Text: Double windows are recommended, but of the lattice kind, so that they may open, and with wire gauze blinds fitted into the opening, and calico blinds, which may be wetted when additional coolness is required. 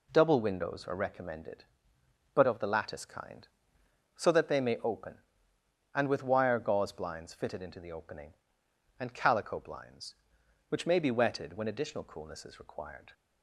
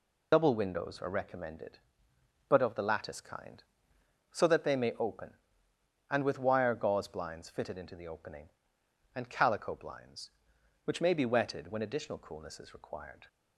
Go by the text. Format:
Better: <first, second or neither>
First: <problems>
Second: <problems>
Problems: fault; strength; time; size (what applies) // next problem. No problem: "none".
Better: first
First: none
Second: loses the start of "Double"; at 0.3 s; 80 ms